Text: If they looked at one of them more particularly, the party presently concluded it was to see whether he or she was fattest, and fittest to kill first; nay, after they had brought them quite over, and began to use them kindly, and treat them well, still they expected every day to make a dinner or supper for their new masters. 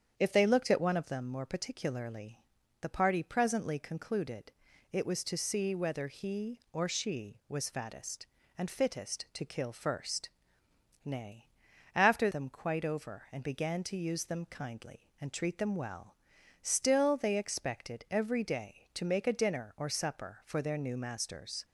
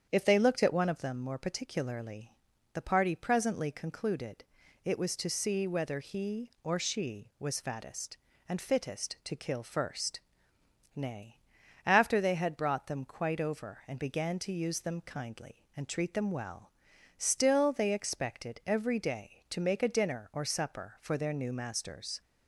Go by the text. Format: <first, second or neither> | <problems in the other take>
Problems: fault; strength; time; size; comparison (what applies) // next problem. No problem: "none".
second | starts louder than the rest; strong; until 1.2 s; 8 dB; strong in the second // pauses between "concluded" and "it"; at 4.5 s; 0.40 s long; also in the second // skips "they had brought"; at 12.3 s